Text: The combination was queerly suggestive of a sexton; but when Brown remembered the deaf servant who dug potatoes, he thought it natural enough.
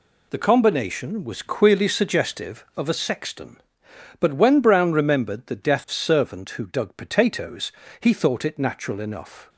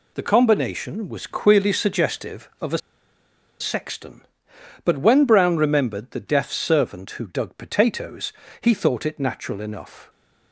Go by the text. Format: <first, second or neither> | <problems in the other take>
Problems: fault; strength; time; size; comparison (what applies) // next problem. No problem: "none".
first | pauses between "a" and "sexton"; noticeable; at 2.7 s; 0.80 s long